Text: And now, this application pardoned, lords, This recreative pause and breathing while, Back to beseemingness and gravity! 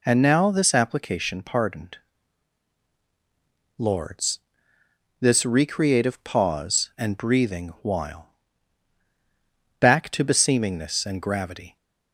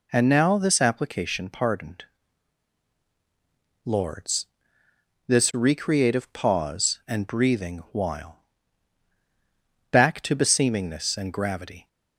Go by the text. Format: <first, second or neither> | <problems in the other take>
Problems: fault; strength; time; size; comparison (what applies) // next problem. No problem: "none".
neither | none